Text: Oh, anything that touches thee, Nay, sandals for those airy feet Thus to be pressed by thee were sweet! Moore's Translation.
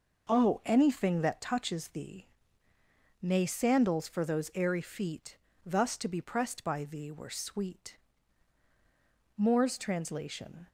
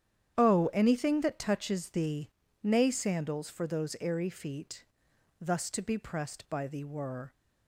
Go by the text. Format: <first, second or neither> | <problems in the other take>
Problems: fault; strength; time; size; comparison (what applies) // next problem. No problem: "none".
first | starts louder than the rest; strong; until 1.3 s; 9.5 dB // pauses between "feet" and "Thus"; noticeable; at 4.8 s; 0.54 s long; slight in the first // stops before "sweet Moore's Translation"; at 7.3 s